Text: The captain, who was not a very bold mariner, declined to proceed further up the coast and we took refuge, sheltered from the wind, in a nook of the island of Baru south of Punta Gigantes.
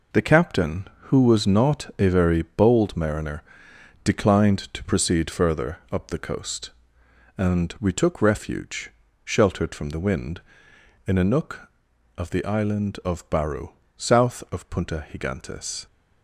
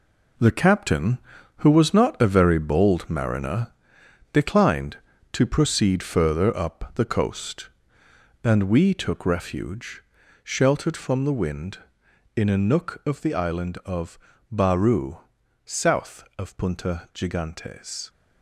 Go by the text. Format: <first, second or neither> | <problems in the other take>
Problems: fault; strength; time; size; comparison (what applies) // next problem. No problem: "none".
first | gets quieter; strong; throughout; 8 dB // pauses between "of" and "Baru"; slight; at 14.1 s; 0.32 s long // pauses between "Baru" and "south"; noticeable; at 15.1 s; 0.48 s long; slight in the first